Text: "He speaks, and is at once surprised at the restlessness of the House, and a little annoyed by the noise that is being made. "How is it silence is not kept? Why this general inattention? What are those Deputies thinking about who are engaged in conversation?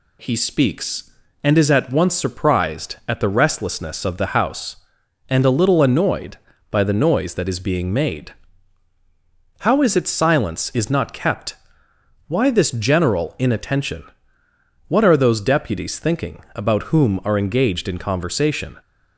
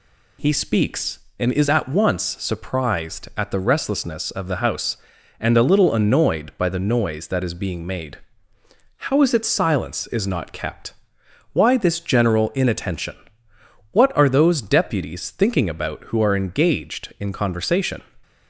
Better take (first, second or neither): second